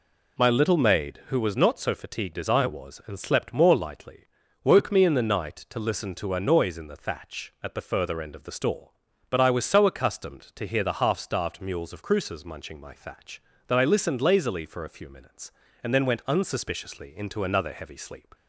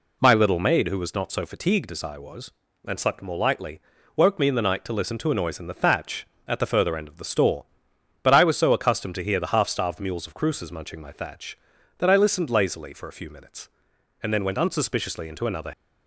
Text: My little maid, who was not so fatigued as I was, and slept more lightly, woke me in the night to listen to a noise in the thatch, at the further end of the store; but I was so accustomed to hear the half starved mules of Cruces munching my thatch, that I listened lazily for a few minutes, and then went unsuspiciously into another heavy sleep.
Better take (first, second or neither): first